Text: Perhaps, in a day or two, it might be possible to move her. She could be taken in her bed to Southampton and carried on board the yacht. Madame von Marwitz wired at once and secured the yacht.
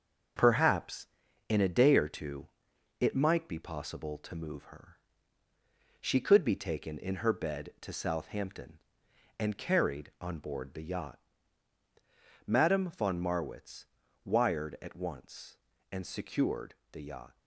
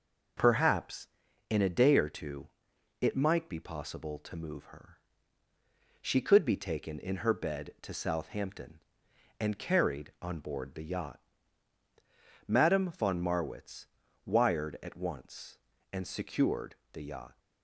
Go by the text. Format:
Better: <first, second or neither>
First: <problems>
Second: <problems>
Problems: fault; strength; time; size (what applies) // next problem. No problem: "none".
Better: second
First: gets quieter; noticeable; throughout; 6 dB // pauses between "Marwitz" and "wired"; at 13.8 s; 0.38 s long // pauses between "secured" and "the"; slight; at 16.7 s; 0.16 s long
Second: pauses between "Marwitz" and "wired"; at 13.8 s; 0.38 s long // pauses between "secured" and "the"; slight; at 16.7 s; 0.16 s long